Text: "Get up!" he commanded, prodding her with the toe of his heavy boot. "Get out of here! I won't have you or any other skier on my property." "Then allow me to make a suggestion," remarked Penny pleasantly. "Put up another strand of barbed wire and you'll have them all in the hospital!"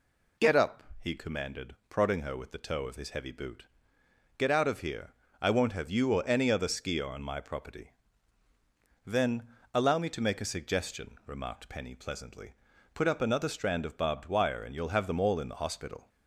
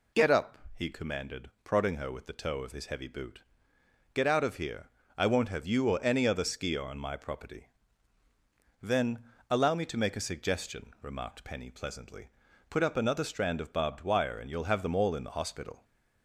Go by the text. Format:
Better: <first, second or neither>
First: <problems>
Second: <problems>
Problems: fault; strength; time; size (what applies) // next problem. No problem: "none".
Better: neither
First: pauses between "Then" and "allow"; slight; at 9.4 s; 0.26 s long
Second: pauses between "Then" and "allow"; slight; at 9.2 s; 0.26 s long